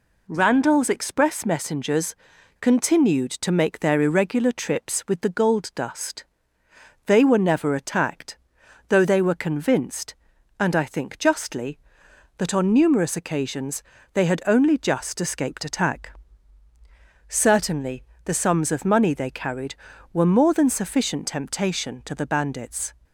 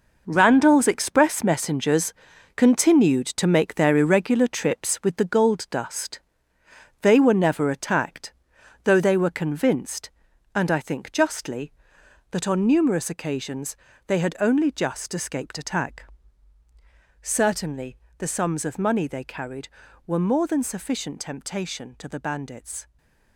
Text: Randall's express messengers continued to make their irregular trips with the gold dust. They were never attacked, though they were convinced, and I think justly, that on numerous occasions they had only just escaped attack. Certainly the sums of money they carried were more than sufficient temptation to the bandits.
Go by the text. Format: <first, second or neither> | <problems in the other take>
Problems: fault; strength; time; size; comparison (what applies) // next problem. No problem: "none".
first | gets quieter; strong; throughout; 10 dB // pauses between "messengers" and "continued"; at 2.1 s; 0.44 s long; noticeable in the first // pauses between "occasions" and "they"; slight; at 13.7 s; 0.32 s long; slight in the first // pauses between "Certainly" and "the"; slight; at 17.9 s; 0.22 s long; slight in the first // stays silent after the last word; slight; from 22.8 s on; 0.5 s long